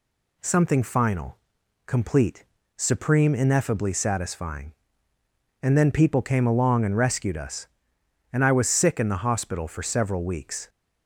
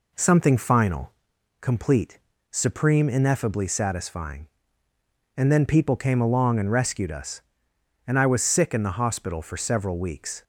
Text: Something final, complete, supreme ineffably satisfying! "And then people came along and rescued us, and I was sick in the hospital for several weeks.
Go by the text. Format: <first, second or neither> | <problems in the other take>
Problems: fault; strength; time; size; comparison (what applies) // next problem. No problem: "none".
first | starts louder than the rest; until 1.3 s; 3.5 dB